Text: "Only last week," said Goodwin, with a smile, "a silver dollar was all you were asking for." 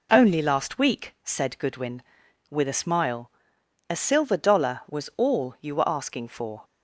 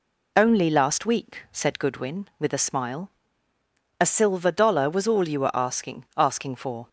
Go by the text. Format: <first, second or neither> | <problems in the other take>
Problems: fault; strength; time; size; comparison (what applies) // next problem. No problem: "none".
first | says "asking" twice; at 6.1 s